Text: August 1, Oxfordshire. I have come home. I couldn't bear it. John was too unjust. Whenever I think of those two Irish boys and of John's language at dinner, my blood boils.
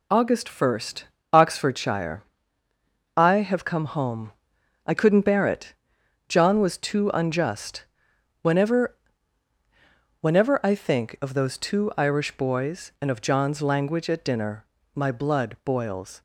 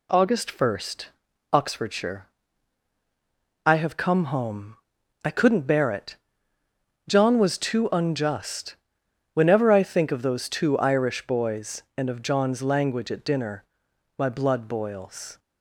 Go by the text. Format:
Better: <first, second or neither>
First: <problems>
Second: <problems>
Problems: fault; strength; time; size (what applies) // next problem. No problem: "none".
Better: second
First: says "Whenever" twice; at 10.2 s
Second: none